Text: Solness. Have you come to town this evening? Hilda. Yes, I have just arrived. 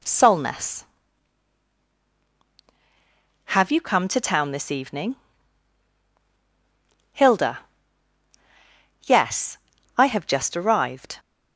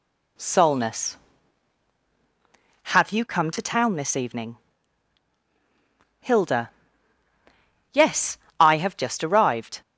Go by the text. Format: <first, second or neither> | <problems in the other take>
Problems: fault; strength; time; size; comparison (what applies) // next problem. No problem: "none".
neither | none